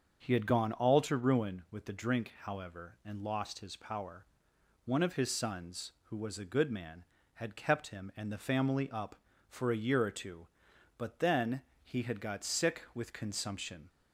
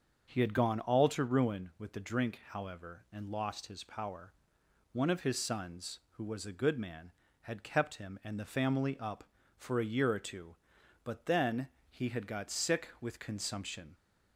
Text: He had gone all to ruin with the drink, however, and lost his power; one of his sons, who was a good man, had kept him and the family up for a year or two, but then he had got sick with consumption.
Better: neither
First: starts louder than the rest; until 1.2 s; 6.5 dB // pauses between "then" and "he"; slight; at 11.6 s; 0.20 s long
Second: starts louder than the rest; until 1.3 s; 6.5 dB // pauses between "then" and "he"; slight; at 11.6 s; 0.20 s long

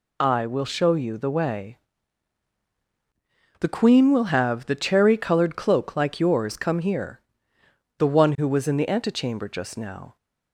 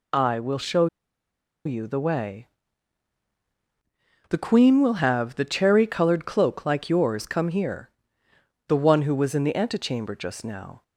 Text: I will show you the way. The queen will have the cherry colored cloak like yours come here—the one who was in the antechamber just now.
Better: first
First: none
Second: pauses between "show" and "you"; noticeable; at 0.8 s; 0.78 s long

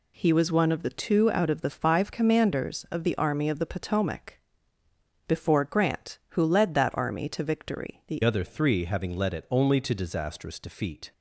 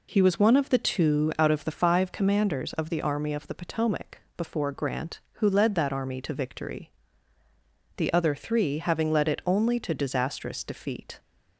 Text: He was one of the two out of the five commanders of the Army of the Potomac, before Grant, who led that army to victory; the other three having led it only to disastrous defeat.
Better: second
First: changes voice at "other"; from 8.2 s on; 2.9 s long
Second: none

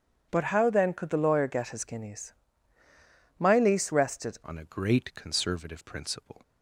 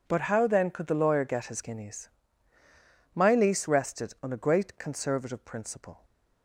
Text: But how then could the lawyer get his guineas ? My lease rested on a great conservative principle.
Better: second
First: changes voice at "on"; from 4.4 s on; 2.0 s long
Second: none

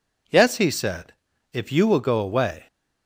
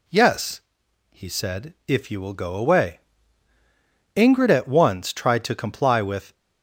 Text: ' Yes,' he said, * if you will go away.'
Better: first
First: none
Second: goes on to say "Ingrid at once tried to comply with"; strong; from 4.1 s on; 2.1 s long

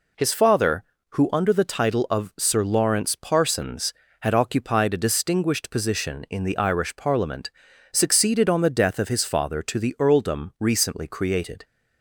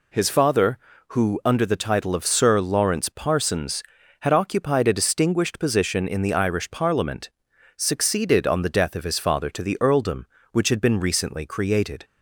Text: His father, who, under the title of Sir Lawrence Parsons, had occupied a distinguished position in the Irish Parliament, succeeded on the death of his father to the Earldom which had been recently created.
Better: second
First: skips "which had been"; at 10.5 s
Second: none

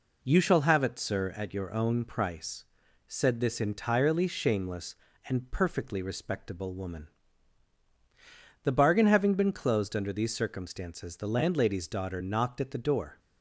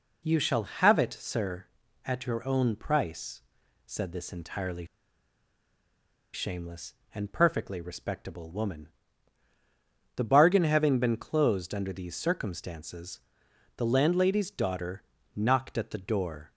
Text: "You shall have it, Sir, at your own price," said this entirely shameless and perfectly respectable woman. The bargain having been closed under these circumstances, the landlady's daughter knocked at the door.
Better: first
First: none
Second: pauses between "entirely" and "shameless"; strong; at 4.8 s; 1.4 s long // pauses between "daughter" and "knocked"; slight; at 15.0 s; 0.32 s long

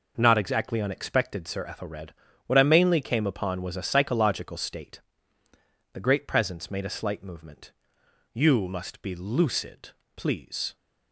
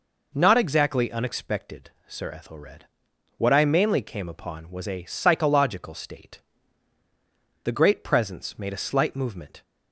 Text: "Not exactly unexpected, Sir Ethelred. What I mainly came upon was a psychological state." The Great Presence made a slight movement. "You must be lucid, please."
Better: first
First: none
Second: stops before "You must be lucid please"; at 9.6 s

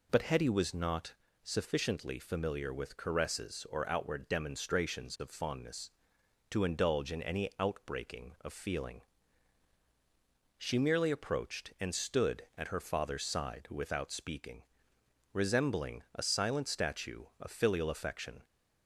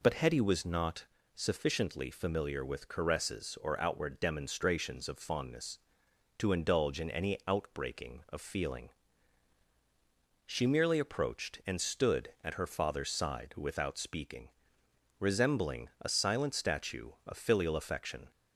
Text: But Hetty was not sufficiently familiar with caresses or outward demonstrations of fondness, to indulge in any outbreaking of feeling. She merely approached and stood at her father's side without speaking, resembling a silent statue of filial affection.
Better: neither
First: pauses between "not" and "sufficiently"; slight; at 1.1 s; 0.30 s long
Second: pauses between "not" and "sufficiently"; slight; at 1.0 s; 0.30 s long

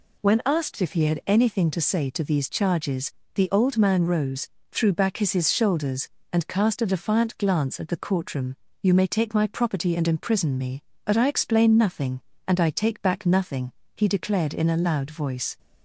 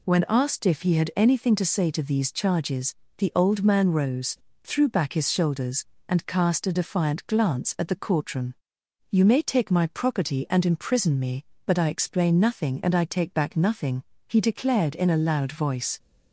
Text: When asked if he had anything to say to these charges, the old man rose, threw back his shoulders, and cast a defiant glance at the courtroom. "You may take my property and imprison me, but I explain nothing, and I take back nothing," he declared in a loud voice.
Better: second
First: says "his" twice; at 5.3 s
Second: none

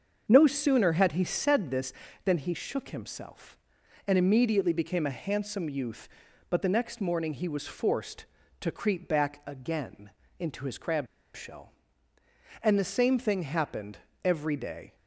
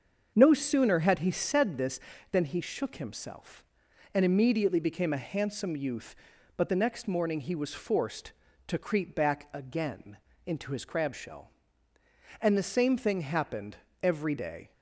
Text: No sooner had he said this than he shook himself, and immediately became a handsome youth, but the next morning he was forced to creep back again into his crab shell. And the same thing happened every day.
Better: second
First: starts louder than the rest; until 1.2 s; 6.5 dB // pauses between "again" and "into"; slight; at 10.0 s; 0.30 s long // pauses between "crab" and "shell"; slight; at 11.0 s; 0.28 s long // pauses between "happened" and "every"; slight; at 13.9 s; 0.26 s long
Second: starts louder than the rest; until 1.3 s; 6.5 dB // pauses between "again" and "into"; slight; at 10.1 s; 0.30 s long // pauses between "happened" and "every"; slight; at 13.7 s; 0.26 s long

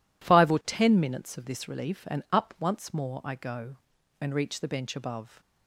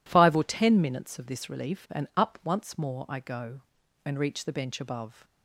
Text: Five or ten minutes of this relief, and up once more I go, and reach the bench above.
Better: neither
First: none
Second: none

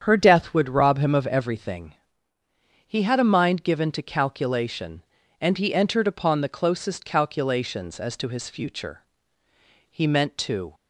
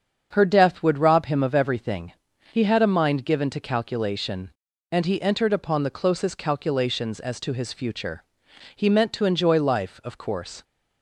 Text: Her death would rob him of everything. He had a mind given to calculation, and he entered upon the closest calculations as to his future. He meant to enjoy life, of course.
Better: second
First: starts louder than the rest; strong; until 1.0 s; 8 dB // stops before "enjoy life of course"; at 10.7 s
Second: starts louder than the rest; strong; until 1.3 s; 7 dB

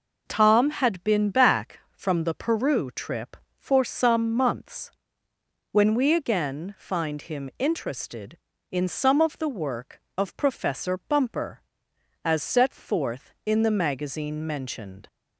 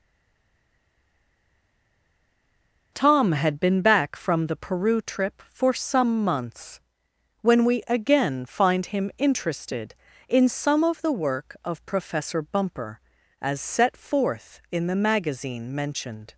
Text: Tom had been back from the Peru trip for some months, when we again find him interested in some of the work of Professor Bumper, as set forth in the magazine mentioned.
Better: first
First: none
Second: stays silent before the first word; strong; until 2.9 s; 2.9 s long

